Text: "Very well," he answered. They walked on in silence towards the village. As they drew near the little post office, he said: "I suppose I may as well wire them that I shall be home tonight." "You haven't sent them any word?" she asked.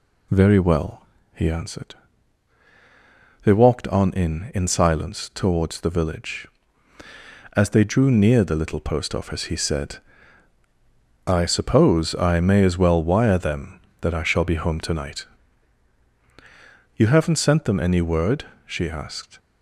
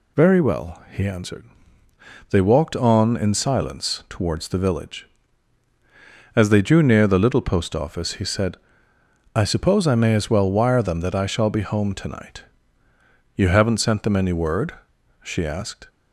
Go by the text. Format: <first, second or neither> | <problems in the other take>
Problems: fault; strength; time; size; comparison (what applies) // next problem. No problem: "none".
second | says "in" twice; at 4.5 s